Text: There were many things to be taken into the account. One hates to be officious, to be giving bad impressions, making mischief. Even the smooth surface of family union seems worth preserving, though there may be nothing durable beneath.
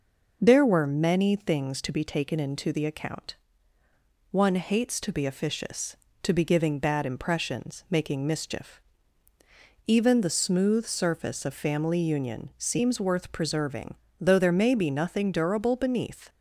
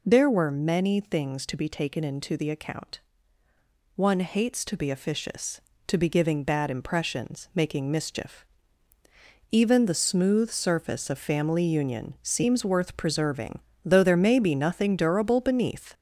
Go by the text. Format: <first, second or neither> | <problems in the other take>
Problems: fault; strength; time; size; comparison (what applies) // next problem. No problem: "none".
first | gets louder; noticeable; throughout; 4.5 dB